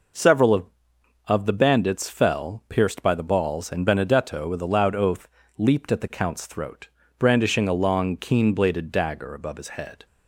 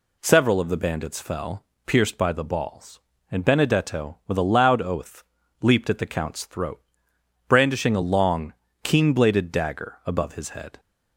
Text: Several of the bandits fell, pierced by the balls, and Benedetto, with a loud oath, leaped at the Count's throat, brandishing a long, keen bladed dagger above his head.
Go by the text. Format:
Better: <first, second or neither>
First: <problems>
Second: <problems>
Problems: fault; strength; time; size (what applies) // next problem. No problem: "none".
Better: second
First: says "of" twice; at 1.2 s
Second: none